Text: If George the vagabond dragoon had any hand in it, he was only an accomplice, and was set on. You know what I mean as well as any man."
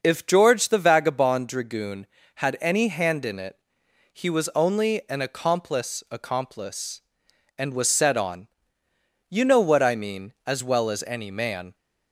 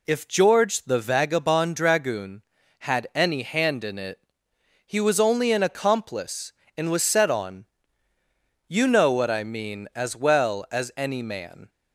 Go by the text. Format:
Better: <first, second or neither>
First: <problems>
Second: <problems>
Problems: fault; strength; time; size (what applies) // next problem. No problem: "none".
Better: second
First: starts louder than the rest; until 1.0 s; 6 dB // says "accomplice" twice; at 6.0 s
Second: none